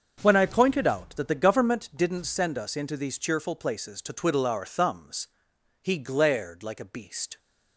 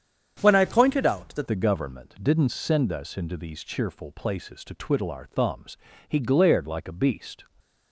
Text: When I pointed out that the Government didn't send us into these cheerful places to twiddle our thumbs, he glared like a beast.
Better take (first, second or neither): first